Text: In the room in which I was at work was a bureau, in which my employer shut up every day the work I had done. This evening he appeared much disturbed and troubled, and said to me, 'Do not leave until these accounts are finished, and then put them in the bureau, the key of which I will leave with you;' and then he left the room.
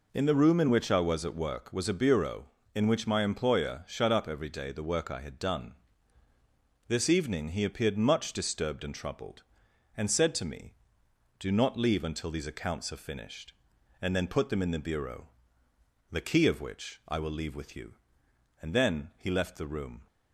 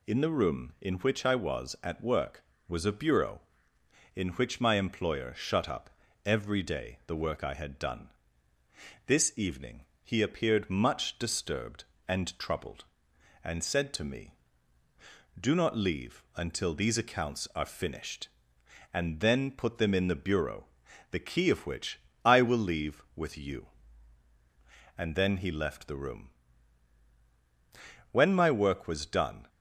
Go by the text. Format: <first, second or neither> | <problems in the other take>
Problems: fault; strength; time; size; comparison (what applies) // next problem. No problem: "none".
first | pauses between "up" and "every"; slight; at 5.8 s; 0.36 s long // pauses between "evening" and "he"; slight; at 9.8 s; 0.18 s long // pauses between "which" and "I"; slight; at 21.9 s; 0.26 s long // goes on to say "When my work was done"; from 28.1 s on; 1.3 s long